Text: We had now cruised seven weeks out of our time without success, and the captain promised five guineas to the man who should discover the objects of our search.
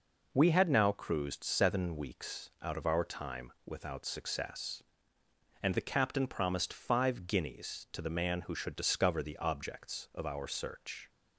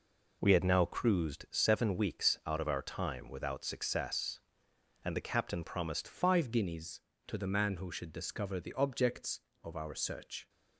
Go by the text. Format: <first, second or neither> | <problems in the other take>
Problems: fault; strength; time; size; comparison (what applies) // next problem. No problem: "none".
first | changes voice at "five"; from 6.0 s on; 4.4 s long